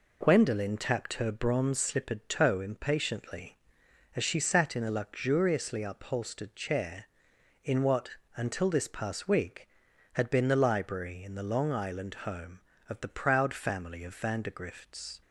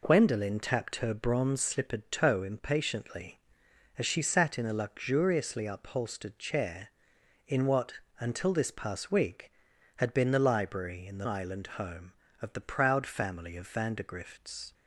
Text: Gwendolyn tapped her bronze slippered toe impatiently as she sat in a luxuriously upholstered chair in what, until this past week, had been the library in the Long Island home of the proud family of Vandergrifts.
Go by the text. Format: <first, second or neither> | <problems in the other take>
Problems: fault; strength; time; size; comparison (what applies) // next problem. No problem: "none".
first | skips "Long"; at 11.2 s